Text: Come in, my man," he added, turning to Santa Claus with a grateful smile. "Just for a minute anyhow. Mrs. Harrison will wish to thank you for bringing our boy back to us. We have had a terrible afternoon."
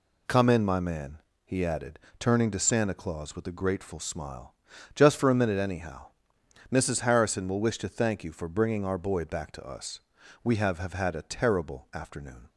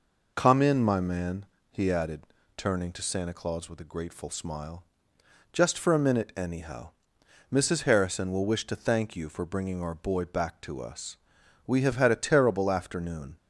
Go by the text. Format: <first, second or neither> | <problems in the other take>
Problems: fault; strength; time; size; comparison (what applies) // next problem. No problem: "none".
second | says "have" twice; at 10.7 s